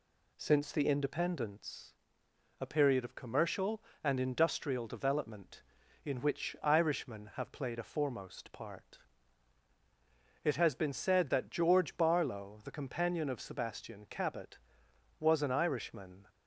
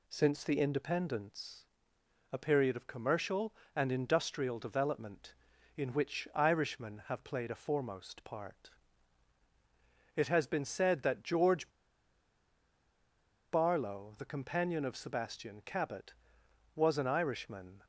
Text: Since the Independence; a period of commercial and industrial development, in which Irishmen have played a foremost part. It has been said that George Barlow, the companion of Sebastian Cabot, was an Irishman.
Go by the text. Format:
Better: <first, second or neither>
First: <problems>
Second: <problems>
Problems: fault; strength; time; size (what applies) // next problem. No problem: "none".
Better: first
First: none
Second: pauses between "George" and "Barlow"; strong; at 11.6 s; 1.8 s long